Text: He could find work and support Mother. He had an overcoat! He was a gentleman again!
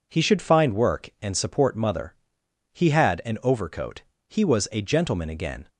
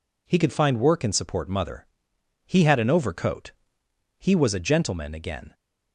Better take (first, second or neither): second